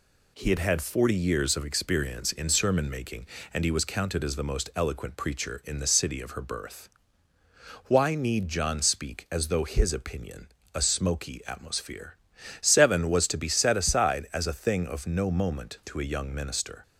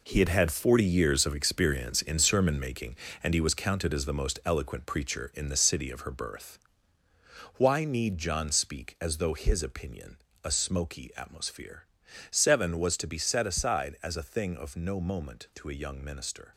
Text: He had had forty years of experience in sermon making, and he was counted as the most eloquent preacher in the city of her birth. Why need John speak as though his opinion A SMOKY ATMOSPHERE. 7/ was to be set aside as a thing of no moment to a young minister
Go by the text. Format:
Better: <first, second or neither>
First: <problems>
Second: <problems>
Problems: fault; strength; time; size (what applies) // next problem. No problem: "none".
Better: first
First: pauses between "opinion" and "A"; slight; at 10.4 s; 0.26 s long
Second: gets quieter; strong; throughout; 9 dB // pauses between "opinion" and "A"; slight; at 10.1 s; 0.26 s long